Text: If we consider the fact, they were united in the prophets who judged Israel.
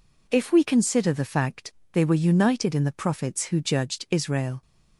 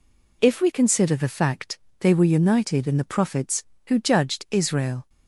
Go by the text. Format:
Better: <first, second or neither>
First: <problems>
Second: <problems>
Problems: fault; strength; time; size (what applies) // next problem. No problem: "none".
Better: neither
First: none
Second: none